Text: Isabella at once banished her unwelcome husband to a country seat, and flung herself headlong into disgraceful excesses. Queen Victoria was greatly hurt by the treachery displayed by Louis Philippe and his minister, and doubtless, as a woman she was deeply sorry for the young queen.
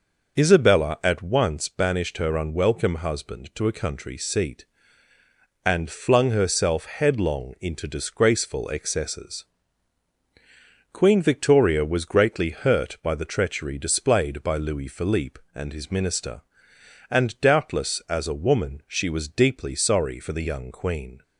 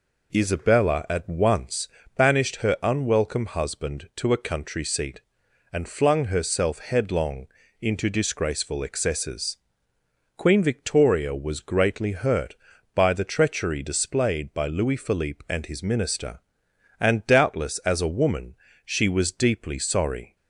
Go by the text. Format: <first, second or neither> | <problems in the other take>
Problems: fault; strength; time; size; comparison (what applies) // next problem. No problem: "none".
first | pauses between "once" and "banished"; slight; at 1.8 s; 0.28 s long // pauses between "headlong" and "into"; slight; at 7.4 s; 0.34 s long // pauses between "woman" and "she"; slight; at 18.5 s; 0.30 s long // stops before "for the young queen"; at 20.3 s